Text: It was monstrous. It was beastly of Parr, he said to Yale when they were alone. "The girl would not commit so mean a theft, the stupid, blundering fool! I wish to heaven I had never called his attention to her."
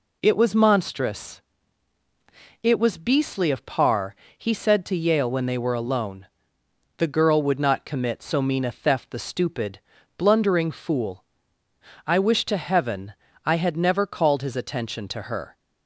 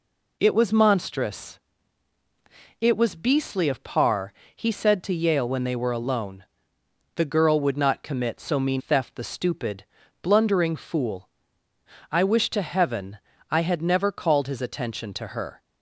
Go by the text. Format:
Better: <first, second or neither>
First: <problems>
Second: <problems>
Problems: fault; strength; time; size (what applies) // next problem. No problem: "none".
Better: first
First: pauses between "heaven" and "I"; slight; at 13.1 s; 0.33 s long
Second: skips "a"; at 8.7 s // pauses between "heaven" and "I"; slight; at 13.1 s; 0.34 s long